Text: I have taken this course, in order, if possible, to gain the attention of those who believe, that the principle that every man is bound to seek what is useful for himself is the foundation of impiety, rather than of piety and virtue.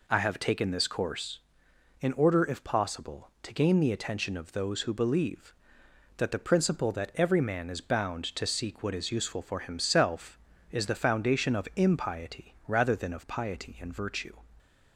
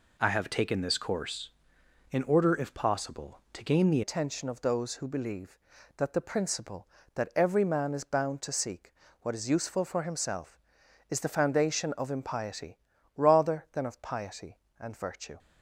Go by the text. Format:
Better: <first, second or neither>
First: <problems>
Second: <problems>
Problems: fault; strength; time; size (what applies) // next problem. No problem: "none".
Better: first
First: none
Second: changes voice at "attention"; from 4.0 s on; 11.3 s long // pauses between "seek" and "what"; slight; at 8.9 s; 0.28 s long